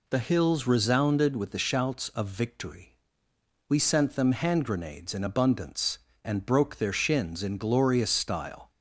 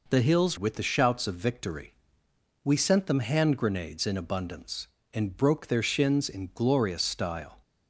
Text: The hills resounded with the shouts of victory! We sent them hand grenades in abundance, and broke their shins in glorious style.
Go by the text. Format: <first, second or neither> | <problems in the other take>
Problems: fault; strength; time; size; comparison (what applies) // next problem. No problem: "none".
first | skips "resounded"; at 0.5 s